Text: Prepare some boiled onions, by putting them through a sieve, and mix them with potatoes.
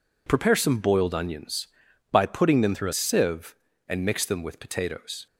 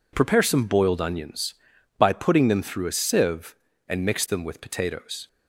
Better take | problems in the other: second | changes voice from "through" to "a"; from 2.7 to 2.9 s; 0.2 s long

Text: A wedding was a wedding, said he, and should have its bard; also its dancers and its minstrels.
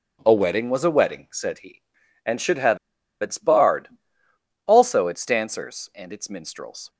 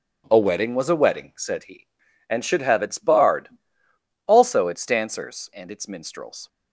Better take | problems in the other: second | pauses between "have" and "its"; at 2.7 s; 0.43 s long

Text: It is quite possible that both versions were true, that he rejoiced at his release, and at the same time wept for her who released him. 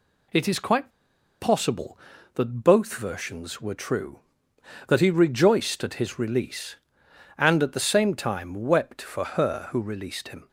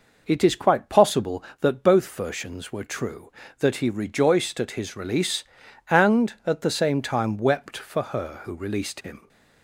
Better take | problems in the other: second | pauses between "quite" and "possible"; noticeable; at 0.9 s; 0.49 s long

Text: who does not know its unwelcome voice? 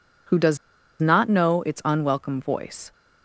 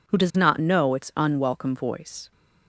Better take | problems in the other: second | pauses between "does" and "not"; at 0.5 s; 0.44 s long

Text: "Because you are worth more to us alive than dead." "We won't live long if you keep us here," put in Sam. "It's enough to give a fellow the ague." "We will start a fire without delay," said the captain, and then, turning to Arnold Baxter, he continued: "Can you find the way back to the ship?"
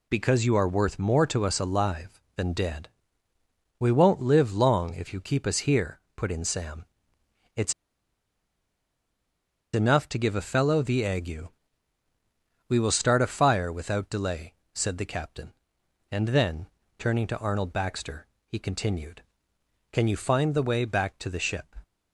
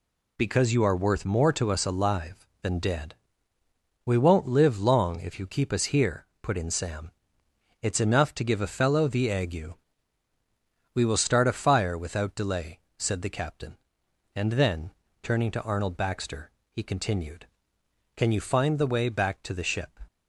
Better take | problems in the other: second | pauses between "It's" and "enough"; strong; at 7.7 s; 2.0 s long

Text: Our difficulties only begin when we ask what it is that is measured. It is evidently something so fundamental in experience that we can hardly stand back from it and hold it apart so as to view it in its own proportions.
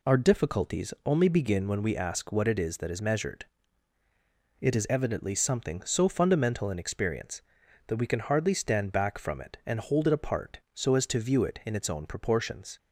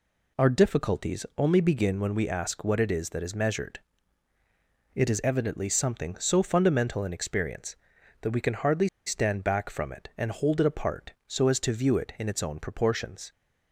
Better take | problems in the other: first | pauses between "hardly" and "stand"; slight; at 8.8 s; 0.18 s long

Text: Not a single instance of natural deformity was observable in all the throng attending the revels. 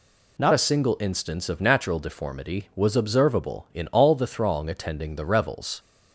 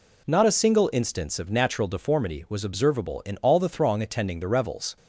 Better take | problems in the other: second | changes voice at "a"; from 0.5 s on; 5.2 s long

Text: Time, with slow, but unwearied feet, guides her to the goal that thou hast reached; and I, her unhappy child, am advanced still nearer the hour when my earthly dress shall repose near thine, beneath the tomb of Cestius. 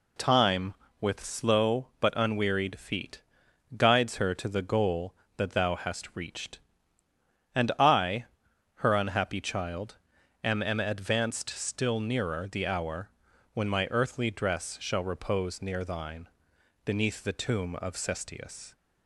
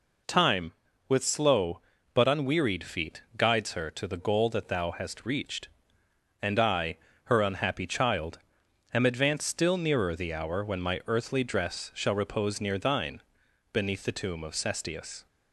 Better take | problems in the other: second | says "am" twice; at 10.6 s // pauses between "hour" and "when"; at 13.1 s; 0.42 s long

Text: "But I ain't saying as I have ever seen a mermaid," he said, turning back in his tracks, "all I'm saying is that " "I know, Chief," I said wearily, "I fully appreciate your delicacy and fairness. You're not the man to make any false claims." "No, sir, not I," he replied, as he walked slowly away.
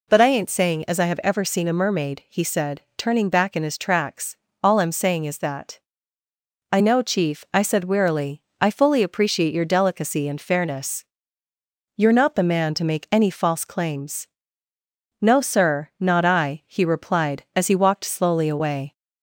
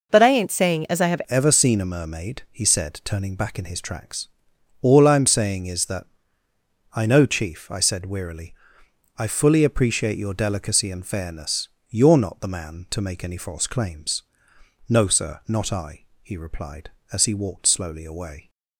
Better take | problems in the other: first | changes voice at "ever"; from 1.2 s on; 17.2 s long

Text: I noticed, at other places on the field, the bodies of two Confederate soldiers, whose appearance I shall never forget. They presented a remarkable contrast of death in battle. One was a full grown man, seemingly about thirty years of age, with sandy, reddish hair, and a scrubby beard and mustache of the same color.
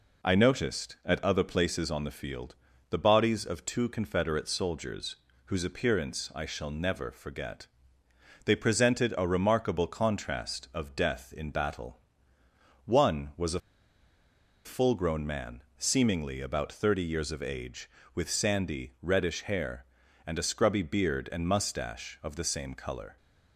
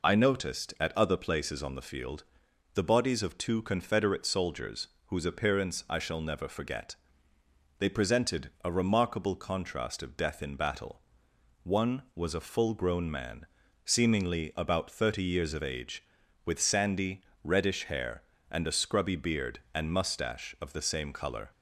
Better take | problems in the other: second | pauses between "a" and "full"; at 13.5 s; 1.0 s long

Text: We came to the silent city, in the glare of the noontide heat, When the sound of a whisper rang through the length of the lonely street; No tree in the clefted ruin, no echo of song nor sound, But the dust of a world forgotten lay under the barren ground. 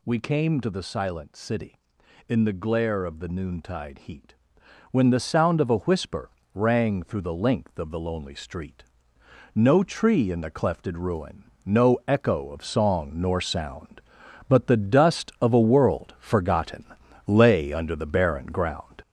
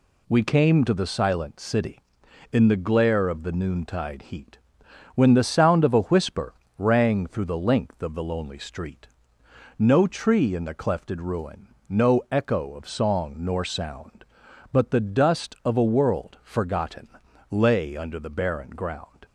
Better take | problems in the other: second | gets louder; noticeable; throughout; 5 dB // pauses between "whisper" and "rang"; slight; at 6.3 s; 0.24 s long; slight in the second // pauses between "forgotten" and "lay"; at 16.8 s; 0.44 s long; also in the second

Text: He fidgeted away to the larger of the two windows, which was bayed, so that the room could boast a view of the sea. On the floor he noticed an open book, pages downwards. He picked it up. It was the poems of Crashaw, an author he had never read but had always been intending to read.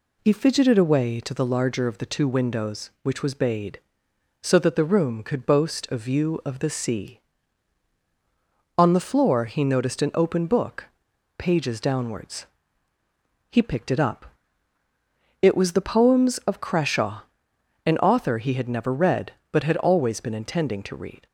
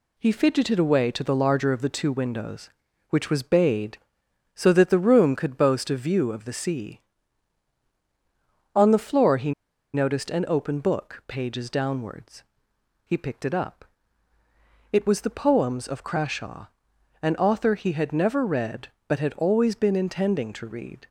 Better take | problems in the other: first | pauses between "he" and "noticed"; at 9.5 s; 0.42 s long

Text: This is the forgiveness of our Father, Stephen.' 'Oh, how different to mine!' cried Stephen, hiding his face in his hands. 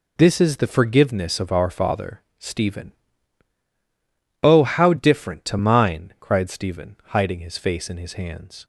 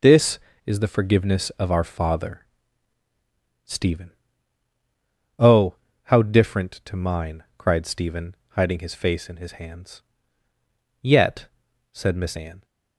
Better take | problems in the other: first | goes on to say "Yet said Miss Anne"; from 11.0 s on; 1.6 s long

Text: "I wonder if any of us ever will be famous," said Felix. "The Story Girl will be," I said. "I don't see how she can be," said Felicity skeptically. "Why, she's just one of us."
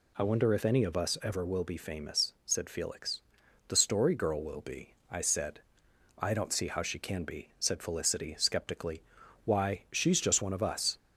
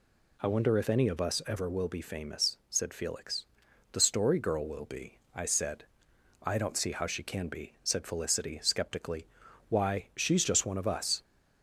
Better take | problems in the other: neither | none

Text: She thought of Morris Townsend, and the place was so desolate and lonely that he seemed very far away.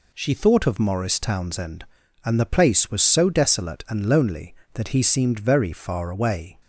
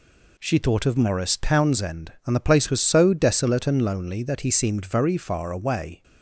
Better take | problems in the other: neither | none

